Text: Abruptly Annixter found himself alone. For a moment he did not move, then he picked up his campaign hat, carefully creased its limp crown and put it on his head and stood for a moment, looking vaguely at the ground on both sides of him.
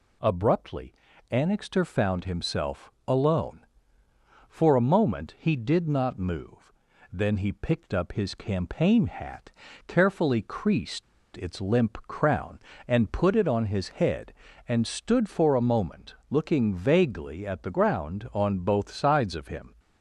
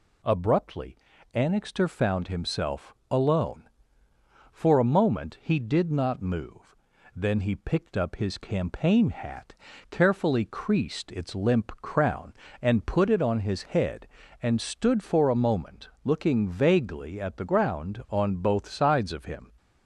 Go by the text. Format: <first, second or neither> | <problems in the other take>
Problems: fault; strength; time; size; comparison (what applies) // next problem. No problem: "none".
second | pauses between "Abruptly" and "Annixter"; at 0.9 s; 0.38 s long; also in the second // pauses between "himself" and "alone"; slight; at 2.9 s; 0.16 s long; slight in the second // pauses between "creased" and "its"; slight; at 11.0 s; 0.32 s long